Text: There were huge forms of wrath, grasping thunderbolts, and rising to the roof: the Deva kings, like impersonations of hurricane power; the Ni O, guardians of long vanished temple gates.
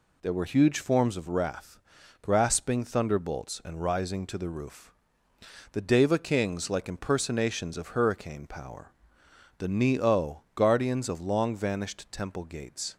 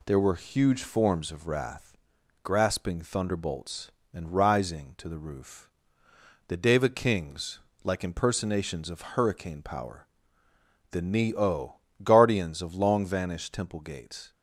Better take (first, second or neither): neither